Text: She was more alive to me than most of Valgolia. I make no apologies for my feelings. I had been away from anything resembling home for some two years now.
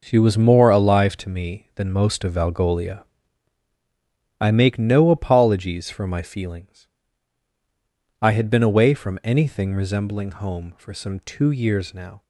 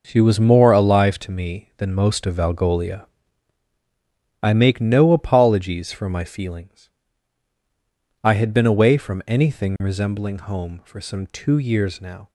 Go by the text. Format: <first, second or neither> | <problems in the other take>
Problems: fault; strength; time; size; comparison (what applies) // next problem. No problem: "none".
neither | none